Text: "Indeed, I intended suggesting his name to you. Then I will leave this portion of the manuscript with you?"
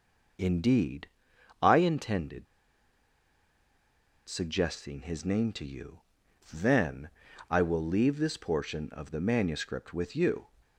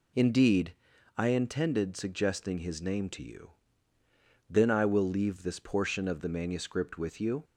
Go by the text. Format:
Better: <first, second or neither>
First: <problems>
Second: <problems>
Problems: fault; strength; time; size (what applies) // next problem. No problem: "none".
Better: second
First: pauses between "intended" and "suggesting"; strong; at 2.4 s; 1.8 s long // pauses between "Then" and "I"; at 7.0 s; 0.40 s long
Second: none